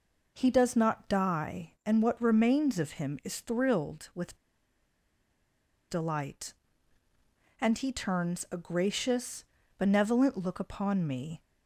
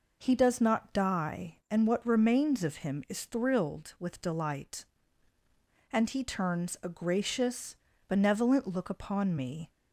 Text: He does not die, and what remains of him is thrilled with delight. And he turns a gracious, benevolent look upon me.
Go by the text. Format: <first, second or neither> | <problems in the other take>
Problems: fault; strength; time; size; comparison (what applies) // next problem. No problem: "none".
second | pauses between "with" and "delight"; strong; at 4.3 s; 1.5 s long